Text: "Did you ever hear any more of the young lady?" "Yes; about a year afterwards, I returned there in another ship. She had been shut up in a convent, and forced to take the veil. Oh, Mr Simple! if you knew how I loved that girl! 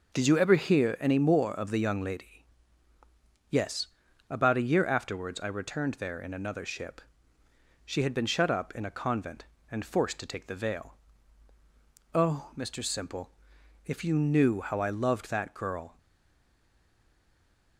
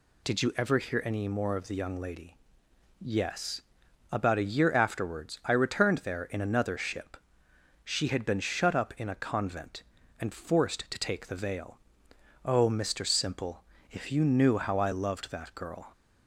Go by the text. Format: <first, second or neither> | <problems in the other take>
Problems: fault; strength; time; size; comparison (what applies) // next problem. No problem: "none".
second | stays silent after the last word; noticeable; from 15.9 s on; 1.8 s long